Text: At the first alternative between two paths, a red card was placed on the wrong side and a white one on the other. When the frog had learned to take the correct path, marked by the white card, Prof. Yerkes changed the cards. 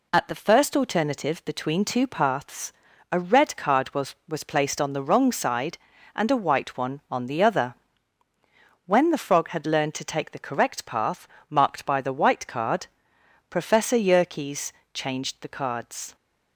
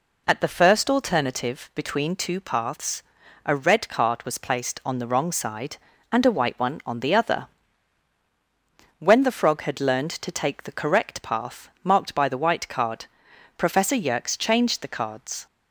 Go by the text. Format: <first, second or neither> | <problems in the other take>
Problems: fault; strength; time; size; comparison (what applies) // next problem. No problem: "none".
second | says "was" twice; at 4.2 s // pauses between "Yerkes" and "changed"; slight; at 14.7 s; 0.24 s long